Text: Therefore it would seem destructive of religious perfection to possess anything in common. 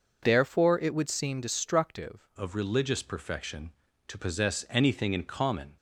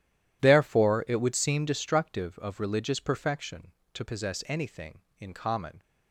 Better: second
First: changes voice at "of"; from 2.3 s on; 3.4 s long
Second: none

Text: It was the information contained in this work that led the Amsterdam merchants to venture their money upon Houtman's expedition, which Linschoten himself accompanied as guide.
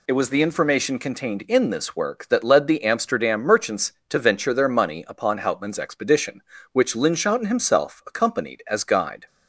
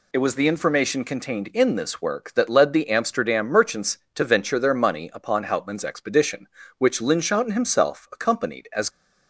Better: first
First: none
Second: stops before "guide"; at 8.8 s

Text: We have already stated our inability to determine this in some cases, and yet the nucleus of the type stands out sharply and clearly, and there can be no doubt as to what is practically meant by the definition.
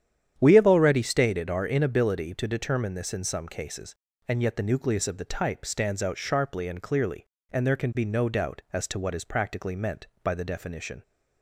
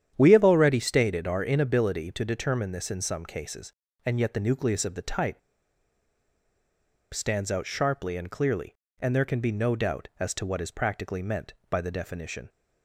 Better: first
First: starts louder than the rest; strong; until 1.3 s; 9.5 dB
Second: starts louder than the rest; strong; until 1.1 s; 9.5 dB // pauses between "type" and "stands"; strong; at 5.3 s; 1.7 s long

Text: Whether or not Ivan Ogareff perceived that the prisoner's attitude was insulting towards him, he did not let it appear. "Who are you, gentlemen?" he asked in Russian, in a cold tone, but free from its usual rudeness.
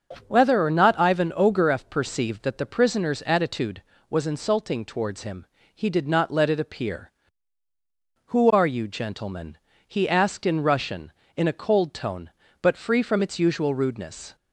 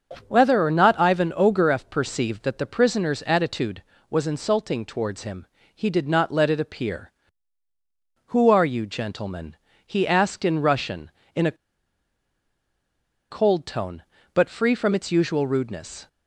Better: first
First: starts louder than the rest; until 1.2 s; 6.5 dB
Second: starts louder than the rest; until 1.2 s; 6 dB // pauses between "a" and "cold"; strong; at 11.5 s; 1.7 s long

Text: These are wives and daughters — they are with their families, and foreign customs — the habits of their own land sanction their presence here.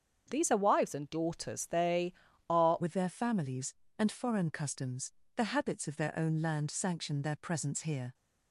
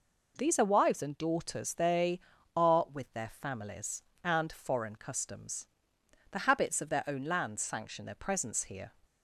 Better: second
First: starts louder than the rest; strong; until 1.3 s; 7 dB // changes voice at "with"; from 2.8 s on; 5.3 s long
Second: none

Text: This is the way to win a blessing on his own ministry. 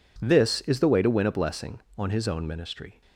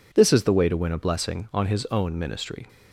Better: neither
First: none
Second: none

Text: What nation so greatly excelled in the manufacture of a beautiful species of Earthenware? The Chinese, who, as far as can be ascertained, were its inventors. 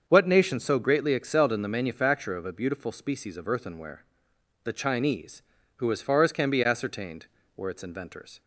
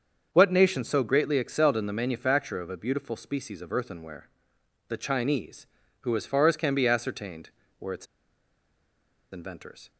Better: first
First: starts louder than the rest; until 1.0 s; 7 dB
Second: starts louder than the rest; until 1.3 s; 6.5 dB // pauses between "its" and "inventors"; strong; at 8.0 s; 1.2 s long

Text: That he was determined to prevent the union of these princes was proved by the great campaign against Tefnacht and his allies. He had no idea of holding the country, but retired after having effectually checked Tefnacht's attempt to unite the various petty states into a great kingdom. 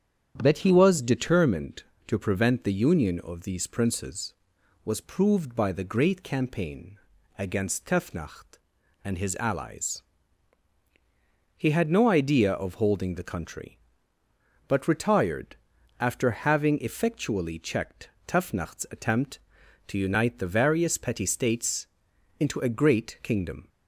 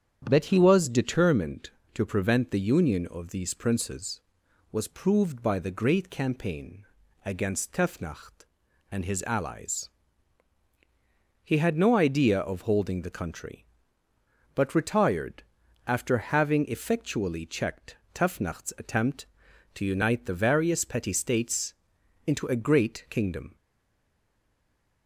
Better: first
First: starts louder than the rest; strong; until 1.4 s; 9 dB // pauses between "campaign" and "against"; at 6.9 s; 0.40 s long // pauses between "retired" and "after"; at 15.5 s; 0.42 s long // pauses between "checked" and "Tefnacht's"; slight; at 18.1 s; 0.18 s long // pauses between "states" and "into"; noticeable; at 21.8 s; 0.52 s long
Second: starts louder than the rest; strong; until 1.3 s; 9 dB // pauses between "campaign" and "against"; at 6.8 s; 0.40 s long // pauses between "retired" and "after"; at 15.4 s; 0.42 s long // pauses between "checked" and "Tefnacht's"; slight; at 17.9 s; 0.18 s long // pauses between "states" and "into"; noticeable; at 21.7 s; 0.52 s long // stays silent after the last word; noticeable; from 23.5 s on; 1.5 s long

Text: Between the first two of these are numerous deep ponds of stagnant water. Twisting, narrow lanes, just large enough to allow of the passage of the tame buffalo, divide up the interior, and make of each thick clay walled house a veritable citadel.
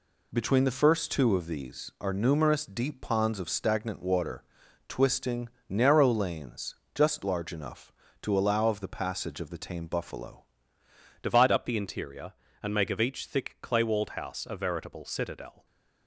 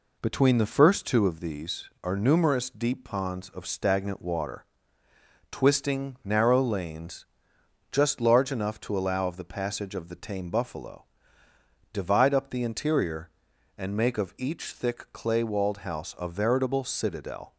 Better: second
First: changes voice at "divide"; from 11.2 s on; 4.4 s long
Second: none

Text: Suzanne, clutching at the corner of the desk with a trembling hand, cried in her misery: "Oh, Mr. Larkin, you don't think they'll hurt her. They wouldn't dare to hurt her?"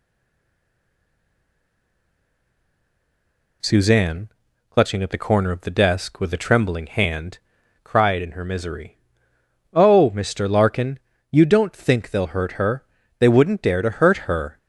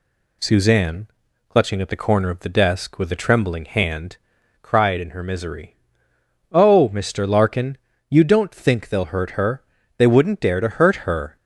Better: second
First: stays silent before the first word; strong; until 3.6 s; 3.6 s long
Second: none

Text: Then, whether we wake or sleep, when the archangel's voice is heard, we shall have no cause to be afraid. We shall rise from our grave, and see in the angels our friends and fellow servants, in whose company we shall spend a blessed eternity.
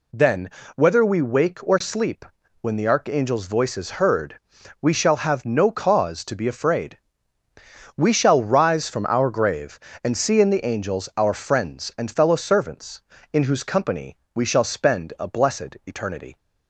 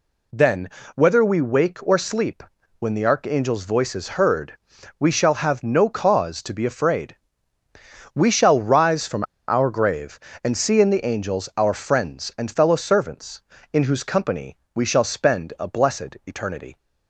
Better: first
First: pauses between "company" and "we"; slight; at 14.1 s; 0.16 s long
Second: pauses between "from" and "our"; slight; at 9.2 s; 0.25 s long // pauses between "company" and "we"; slight; at 14.5 s; 0.16 s long

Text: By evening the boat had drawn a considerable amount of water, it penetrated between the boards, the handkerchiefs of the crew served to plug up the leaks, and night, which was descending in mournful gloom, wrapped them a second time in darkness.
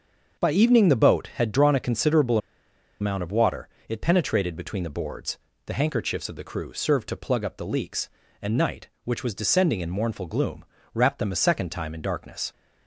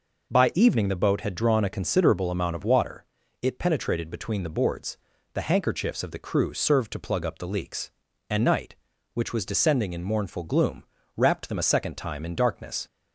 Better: second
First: starts louder than the rest; until 1.4 s; 6.5 dB // pauses between "considerable" and "amount"; noticeable; at 2.3 s; 0.63 s long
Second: none

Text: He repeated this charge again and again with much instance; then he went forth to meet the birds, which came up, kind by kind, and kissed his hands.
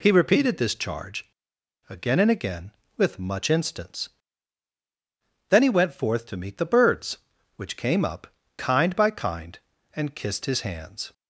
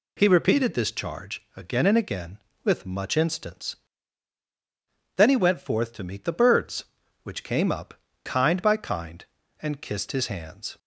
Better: second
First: pauses between "charge" and "again"; noticeable; at 1.2 s; 0.59 s long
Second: none

